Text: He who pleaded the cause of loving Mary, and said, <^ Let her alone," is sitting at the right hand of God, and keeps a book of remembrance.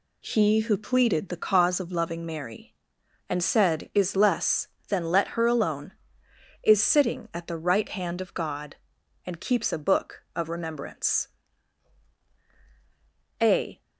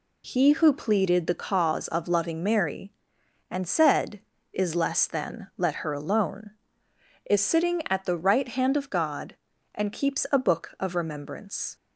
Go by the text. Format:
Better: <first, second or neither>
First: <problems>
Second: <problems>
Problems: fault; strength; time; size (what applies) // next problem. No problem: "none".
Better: second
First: goes on to say "A"; slight; from 13.4 s on; 0.40 s long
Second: none